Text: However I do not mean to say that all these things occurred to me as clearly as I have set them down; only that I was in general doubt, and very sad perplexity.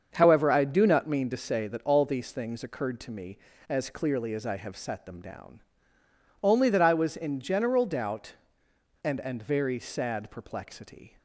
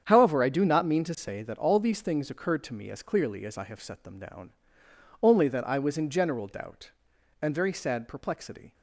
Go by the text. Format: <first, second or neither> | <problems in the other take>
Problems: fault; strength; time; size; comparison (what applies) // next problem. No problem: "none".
second | starts louder than the rest; until 1.1 s; 7 dB; strong in the second // says "and" twice; at 9.2 s